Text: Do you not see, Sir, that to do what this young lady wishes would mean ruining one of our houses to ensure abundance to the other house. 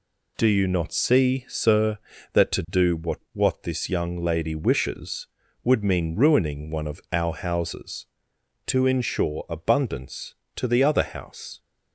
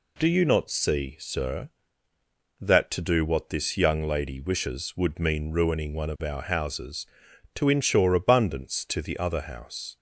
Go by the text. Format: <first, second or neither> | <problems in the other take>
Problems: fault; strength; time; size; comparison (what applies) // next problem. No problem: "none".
second | says "what" twice; at 3.3 s